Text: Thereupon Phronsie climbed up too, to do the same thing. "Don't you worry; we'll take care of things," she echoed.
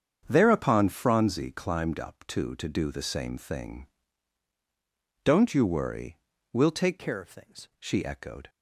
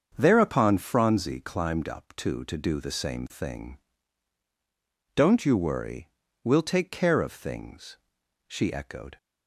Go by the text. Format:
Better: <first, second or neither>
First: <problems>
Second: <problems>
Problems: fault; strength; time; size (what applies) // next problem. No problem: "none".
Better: second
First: starts louder than the rest; strong; until 1.2 s; 7.5 dB // changes voice from "care" to "things"; from 6.9 to 7.6 s; 0.7 s long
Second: starts louder than the rest; until 1.1 s; 7 dB